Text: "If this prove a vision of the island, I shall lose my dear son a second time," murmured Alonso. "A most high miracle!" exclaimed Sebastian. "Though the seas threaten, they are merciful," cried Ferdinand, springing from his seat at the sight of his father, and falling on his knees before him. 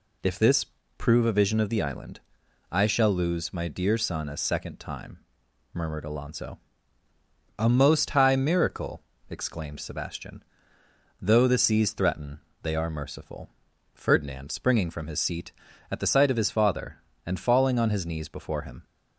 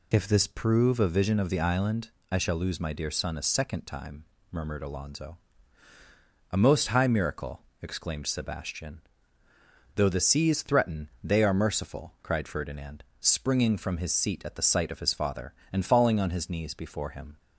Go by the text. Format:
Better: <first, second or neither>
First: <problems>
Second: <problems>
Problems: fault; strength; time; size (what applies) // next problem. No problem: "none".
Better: second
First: pauses between "this" and "prove"; slight; at 0.6 s; 0.32 s long // skips "cried"; at 13.7 s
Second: none